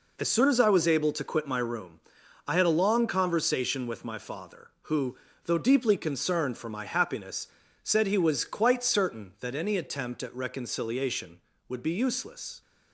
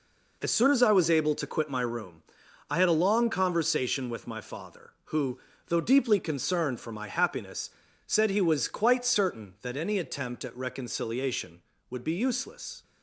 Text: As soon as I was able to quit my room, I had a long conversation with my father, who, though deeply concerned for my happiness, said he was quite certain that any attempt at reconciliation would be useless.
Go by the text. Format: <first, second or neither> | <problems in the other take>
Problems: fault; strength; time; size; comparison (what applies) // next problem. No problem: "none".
neither | none